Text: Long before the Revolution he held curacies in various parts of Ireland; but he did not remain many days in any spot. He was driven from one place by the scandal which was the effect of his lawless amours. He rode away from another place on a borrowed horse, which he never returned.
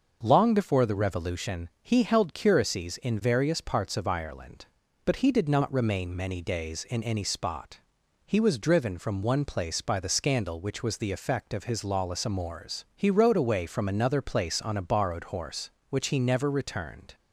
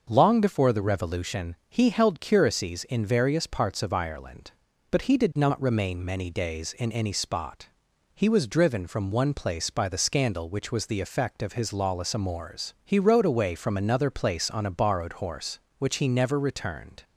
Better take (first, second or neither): neither